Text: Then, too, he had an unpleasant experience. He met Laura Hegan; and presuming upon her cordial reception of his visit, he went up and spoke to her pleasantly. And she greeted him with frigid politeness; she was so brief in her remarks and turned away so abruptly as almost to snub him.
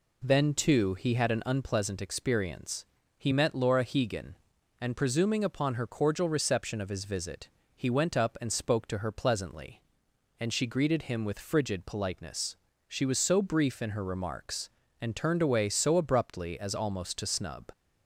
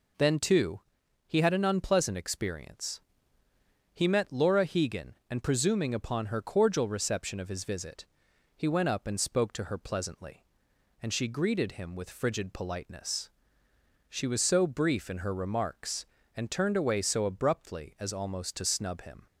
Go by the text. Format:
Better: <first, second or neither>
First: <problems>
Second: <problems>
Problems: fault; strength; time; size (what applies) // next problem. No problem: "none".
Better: second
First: stops before "him"; at 17.7 s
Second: none